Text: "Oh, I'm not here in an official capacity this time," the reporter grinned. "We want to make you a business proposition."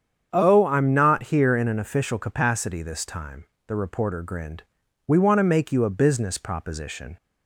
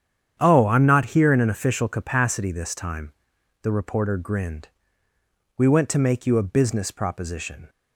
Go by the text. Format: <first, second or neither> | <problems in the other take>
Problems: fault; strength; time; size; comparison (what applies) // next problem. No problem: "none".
first | starts louder than the rest; strong; until 1.4 s; 9 dB; strong in the first // says "went" for "want"; at 5.6 s